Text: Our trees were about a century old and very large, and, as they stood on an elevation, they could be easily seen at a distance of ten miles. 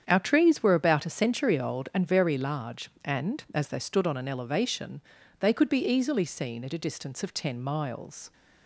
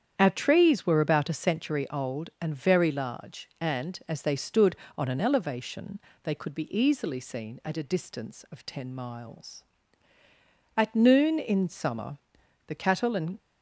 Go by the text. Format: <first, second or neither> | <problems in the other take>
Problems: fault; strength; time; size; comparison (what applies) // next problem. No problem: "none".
first | starts louder than the rest; strong; until 1.1 s; 8.5 dB; strong in the first // goes on to say "At noon in summer the cattle and"; strong; from 10.7 s on; 2.6 s long